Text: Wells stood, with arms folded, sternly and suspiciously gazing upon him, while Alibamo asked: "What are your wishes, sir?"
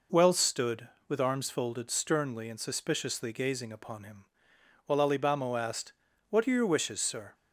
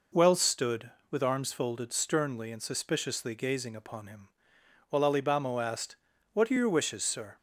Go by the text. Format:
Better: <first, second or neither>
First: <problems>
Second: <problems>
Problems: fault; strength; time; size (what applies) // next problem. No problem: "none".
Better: neither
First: none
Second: none